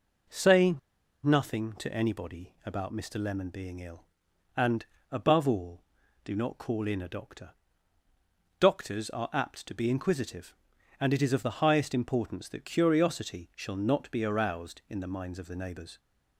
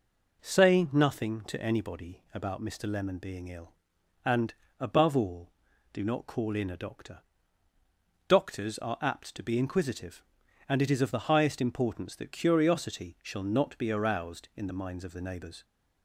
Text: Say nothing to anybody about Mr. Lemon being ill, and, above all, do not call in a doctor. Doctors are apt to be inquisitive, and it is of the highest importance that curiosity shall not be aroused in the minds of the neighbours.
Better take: second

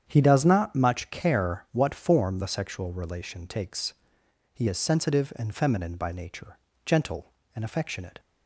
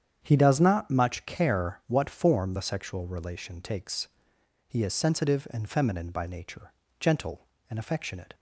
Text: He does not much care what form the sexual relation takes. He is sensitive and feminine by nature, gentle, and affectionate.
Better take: neither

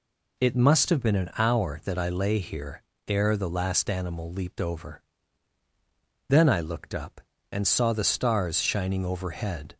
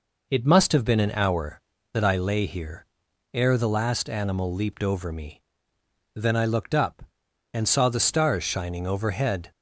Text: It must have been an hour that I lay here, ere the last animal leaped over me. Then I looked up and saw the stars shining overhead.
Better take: second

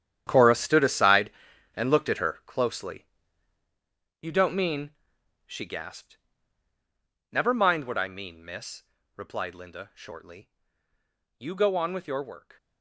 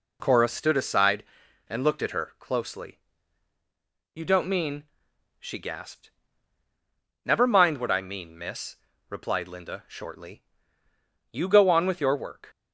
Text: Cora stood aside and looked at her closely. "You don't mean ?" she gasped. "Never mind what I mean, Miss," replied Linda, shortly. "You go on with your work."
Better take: second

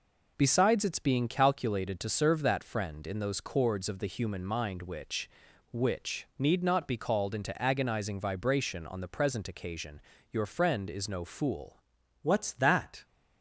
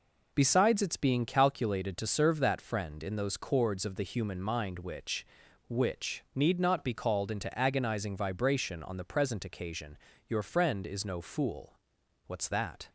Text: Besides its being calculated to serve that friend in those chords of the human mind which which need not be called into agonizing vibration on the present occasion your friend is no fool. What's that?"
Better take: second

